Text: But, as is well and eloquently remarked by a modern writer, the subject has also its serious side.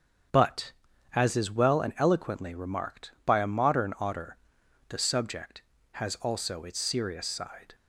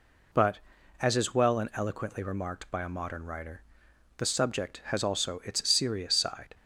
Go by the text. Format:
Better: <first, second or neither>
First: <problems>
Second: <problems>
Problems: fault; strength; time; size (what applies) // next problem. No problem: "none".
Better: second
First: starts louder than the rest; strong; until 1.7 s; 8 dB // says "otter" for "writer"; at 3.9 s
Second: none